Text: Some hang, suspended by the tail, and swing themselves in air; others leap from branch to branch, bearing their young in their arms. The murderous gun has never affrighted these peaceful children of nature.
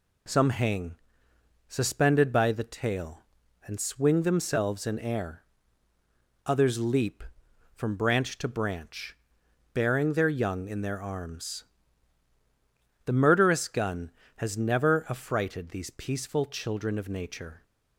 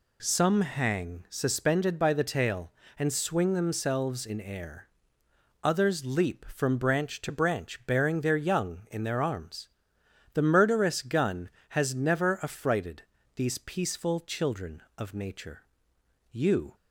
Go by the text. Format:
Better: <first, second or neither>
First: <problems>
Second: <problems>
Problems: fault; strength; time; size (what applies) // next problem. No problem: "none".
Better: first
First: none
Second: pauses between "affrighted" and "these"; slight; at 13.0 s; 0.34 s long // goes on to say "You"; slight; from 16.3 s on; 0.44 s long